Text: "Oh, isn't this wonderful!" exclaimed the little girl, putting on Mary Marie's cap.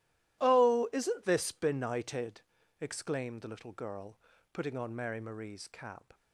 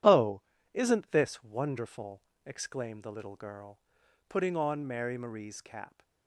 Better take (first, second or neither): second